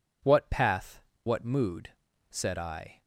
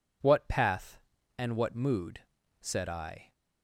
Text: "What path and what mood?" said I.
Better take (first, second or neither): second